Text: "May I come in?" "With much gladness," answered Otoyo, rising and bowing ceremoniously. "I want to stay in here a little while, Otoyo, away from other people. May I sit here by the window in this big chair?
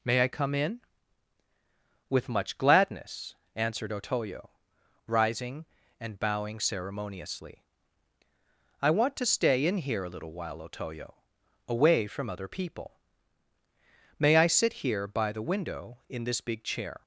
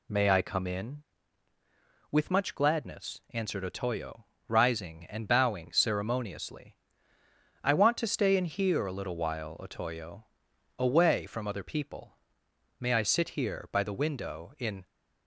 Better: first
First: none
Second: stops before "this big chair"; at 14.8 s

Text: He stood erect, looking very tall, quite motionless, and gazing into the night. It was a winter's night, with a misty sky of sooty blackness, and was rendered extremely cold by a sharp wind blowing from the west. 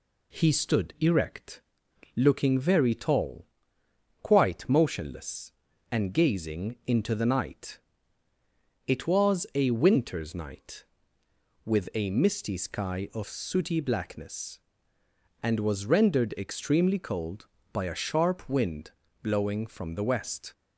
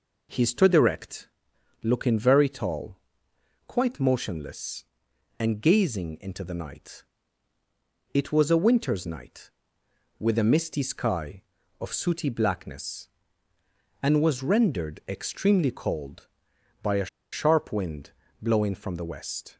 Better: first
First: pauses between "wind" and "blowing"; slight; at 18.9 s; 0.32 s long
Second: pauses between "a" and "sharp"; slight; at 17.0 s; 0.25 s long // pauses between "wind" and "blowing"; slight; at 18.1 s; 0.28 s long

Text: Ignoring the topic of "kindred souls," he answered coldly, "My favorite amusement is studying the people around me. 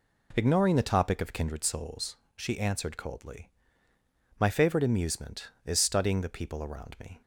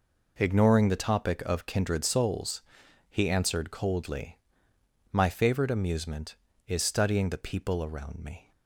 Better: second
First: says "she" for "he"; at 2.3 s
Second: none

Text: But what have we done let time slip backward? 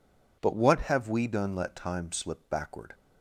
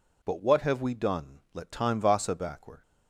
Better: first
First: none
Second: says "vasa" for "slip"; at 2.0 s

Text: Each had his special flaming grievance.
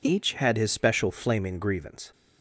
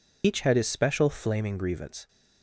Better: first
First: none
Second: loses the start of "Each"; at 0.2 s; 70 ms

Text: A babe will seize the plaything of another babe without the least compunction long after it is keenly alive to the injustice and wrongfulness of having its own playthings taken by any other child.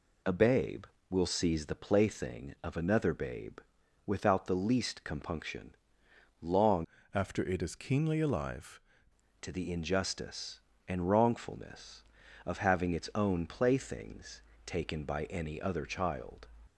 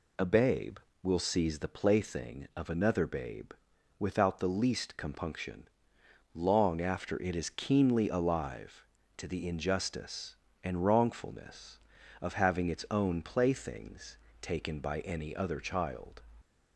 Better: second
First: pauses between "babe" and "without"; noticeable; at 3.5 s; 0.48 s long // pauses between "compunction" and "long"; noticeable; at 5.7 s; 0.66 s long // changes voice from "after" to "alive"; from 7.1 to 8.7 s; 1.6 s long // pauses between "playthings" and "taken"; slight; at 14.4 s; 0.24 s long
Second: pauses between "babe" and "without"; noticeable; at 3.5 s; 0.48 s long // pauses between "compunction" and "long"; noticeable; at 5.6 s; 0.66 s long // pauses between "playthings" and "taken"; slight; at 14.1 s; 0.24 s long

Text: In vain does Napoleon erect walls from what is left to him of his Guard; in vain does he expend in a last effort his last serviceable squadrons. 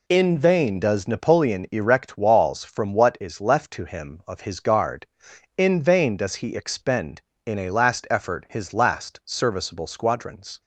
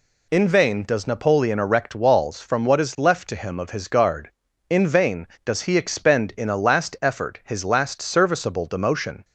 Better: first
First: none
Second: says "demotion" for "squadrons"; at 8.6 s

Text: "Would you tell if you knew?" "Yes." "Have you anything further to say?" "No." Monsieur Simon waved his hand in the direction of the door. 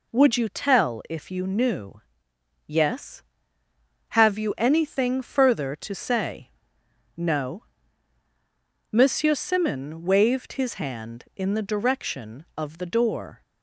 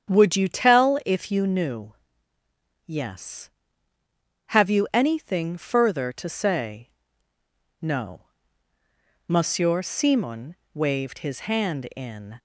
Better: first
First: none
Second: starts louder than the rest; strong; until 1.1 s; 8.5 dB // pauses between "Simon" and "waved"; slight; at 10.5 s; 0.16 s long // stops before "the direction of the door"; at 12.3 s

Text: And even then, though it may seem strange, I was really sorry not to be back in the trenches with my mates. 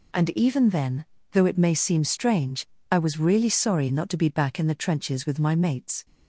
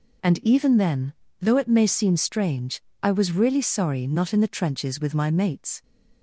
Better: first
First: none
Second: skips "to be back"; at 4.3 s

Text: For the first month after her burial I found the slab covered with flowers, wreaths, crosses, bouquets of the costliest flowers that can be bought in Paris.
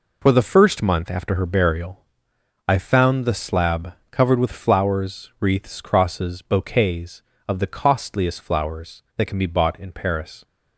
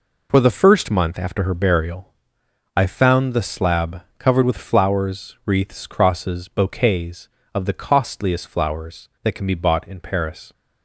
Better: neither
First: pauses between "burial" and "I"; noticeable; at 2.0 s; 0.64 s long // pauses between "slab" and "covered"; slight; at 3.9 s; 0.18 s long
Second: pauses between "burial" and "I"; noticeable; at 2.1 s; 0.64 s long // pauses between "slab" and "covered"; slight; at 4.0 s; 0.17 s long

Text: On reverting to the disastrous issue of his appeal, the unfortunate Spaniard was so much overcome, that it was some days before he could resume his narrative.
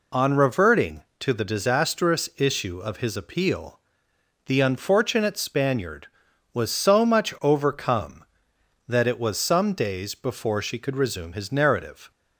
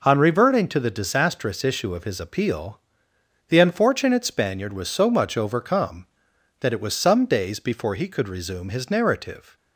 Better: second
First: says "she" for "he"; at 10.6 s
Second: none

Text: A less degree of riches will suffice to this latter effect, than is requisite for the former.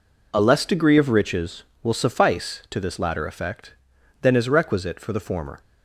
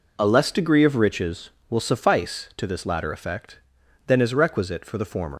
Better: first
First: none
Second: leaves "former" unfinished; at 5.3 s; 80 ms

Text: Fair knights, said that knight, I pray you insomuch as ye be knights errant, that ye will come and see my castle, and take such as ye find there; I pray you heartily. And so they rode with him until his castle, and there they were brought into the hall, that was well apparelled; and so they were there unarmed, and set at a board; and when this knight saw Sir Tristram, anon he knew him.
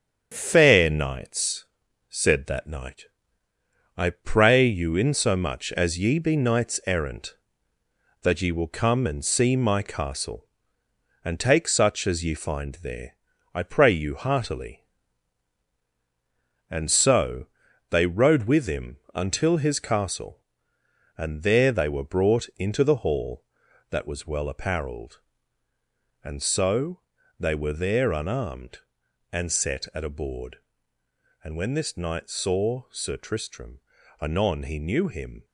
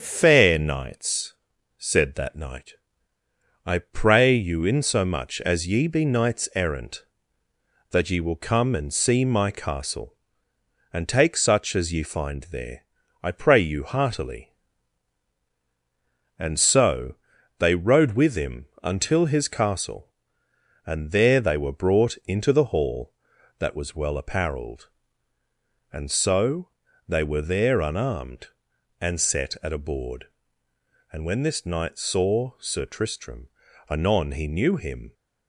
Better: second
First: gets quieter; noticeable; throughout; 5 dB // starts louder than the rest; strong; until 1.3 s; 8 dB // pauses between "so" and "they"; noticeable; at 17.4 s; 0.46 s long // pauses between "him" and "until"; slight; at 18.9 s; 0.16 s long // pauses between "so" and "they"; at 27.0 s; 0.38 s long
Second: starts louder than the rest; strong; until 1.0 s; 7.5 dB // pauses between "so" and "they"; noticeable; at 17.1 s; 0.46 s long // pauses between "him" and "until"; slight; at 18.6 s; 0.16 s long // pauses between "so" and "they"; at 26.6 s; 0.38 s long

